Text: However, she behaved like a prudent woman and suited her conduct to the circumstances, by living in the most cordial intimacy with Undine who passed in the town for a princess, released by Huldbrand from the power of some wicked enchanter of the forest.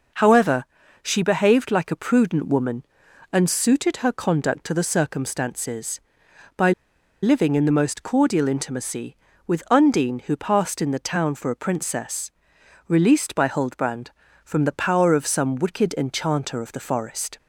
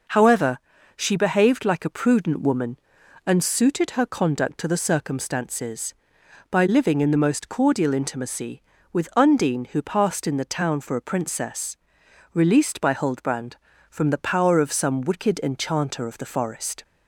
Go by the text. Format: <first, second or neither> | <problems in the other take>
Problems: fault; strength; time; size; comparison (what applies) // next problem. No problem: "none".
second | pauses between "by" and "living"; noticeable; at 6.7 s; 0.51 s long